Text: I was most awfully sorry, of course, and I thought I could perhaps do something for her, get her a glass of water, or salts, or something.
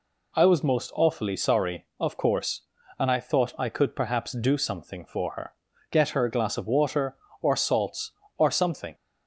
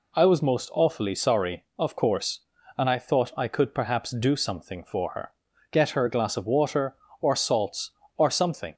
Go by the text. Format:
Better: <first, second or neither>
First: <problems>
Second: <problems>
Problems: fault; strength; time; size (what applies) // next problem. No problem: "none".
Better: neither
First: none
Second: none